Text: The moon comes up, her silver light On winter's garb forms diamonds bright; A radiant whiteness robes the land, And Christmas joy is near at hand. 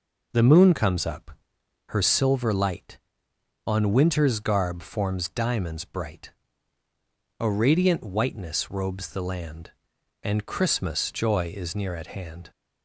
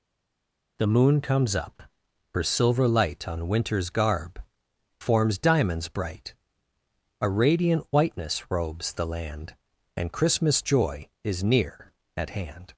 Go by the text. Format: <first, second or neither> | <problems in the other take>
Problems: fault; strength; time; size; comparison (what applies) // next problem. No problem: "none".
first | stays silent before the first word; slight; until 0.7 s; 0.7 s long // pauses between "garb" and "forms"; noticeable; at 4.4 s; 0.58 s long